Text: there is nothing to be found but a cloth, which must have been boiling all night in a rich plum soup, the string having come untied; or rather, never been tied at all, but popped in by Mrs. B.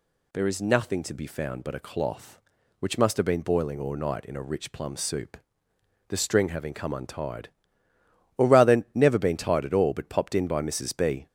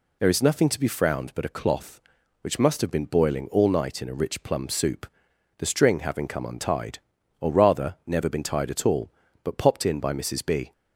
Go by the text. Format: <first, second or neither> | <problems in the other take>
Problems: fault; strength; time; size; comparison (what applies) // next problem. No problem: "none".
first | says "frowned" for "found"; at 0.8 s